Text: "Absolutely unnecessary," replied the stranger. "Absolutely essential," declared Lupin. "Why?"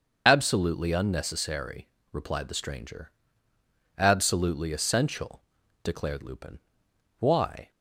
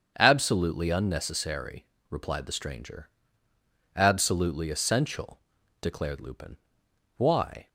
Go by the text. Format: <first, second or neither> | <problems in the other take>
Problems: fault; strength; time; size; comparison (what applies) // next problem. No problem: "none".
second | loses the start of "Absolutely"; at 0.2 s; 75 ms // starts louder than the rest; until 1.2 s; 6.5 dB; strong in the second